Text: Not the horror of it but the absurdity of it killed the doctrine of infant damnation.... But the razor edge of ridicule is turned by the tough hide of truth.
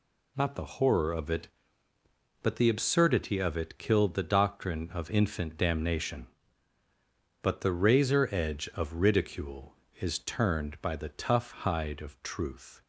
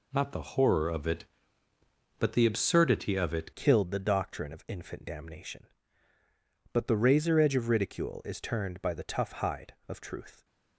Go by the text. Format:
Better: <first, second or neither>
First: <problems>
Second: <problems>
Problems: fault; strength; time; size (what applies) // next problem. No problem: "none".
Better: first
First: none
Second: changes voice at "killed"; from 3.5 s on; 6.9 s long